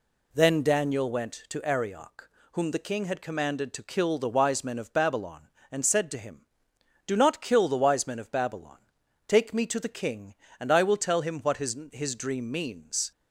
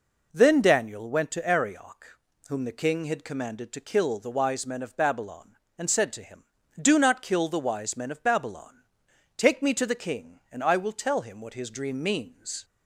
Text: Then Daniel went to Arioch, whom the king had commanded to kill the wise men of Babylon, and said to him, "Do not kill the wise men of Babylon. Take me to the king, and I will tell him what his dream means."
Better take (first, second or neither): second